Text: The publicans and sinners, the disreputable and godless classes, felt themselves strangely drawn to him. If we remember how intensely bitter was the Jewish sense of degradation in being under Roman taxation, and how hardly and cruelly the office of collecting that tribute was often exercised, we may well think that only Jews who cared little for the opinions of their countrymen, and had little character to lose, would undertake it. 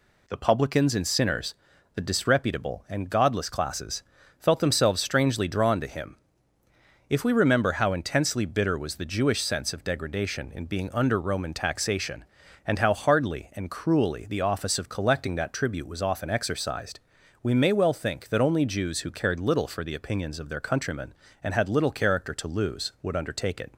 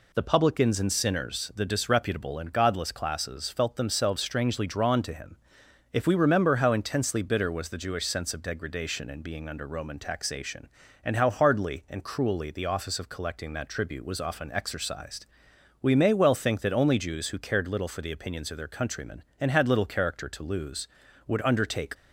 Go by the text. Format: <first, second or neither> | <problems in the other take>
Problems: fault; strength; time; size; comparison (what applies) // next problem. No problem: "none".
first | stops before "it"; at 21.9 s